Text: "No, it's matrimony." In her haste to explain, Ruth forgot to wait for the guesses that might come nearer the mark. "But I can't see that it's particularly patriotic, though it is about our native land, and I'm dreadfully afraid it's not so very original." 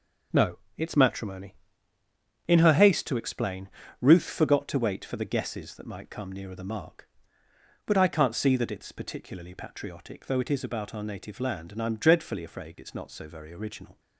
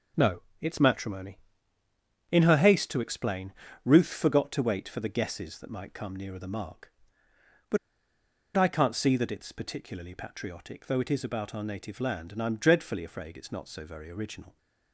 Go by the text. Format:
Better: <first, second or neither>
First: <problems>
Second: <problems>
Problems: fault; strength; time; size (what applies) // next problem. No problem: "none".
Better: first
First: none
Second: pauses between "But" and "I"; noticeable; at 7.7 s; 0.78 s long